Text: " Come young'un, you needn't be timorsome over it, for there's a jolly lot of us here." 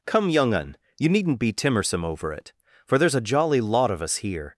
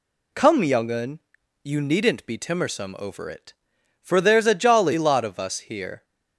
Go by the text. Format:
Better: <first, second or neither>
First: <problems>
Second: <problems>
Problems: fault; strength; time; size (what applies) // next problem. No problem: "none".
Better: second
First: changes voice at "Come"; from 0.0 s on; 4.5 s long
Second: none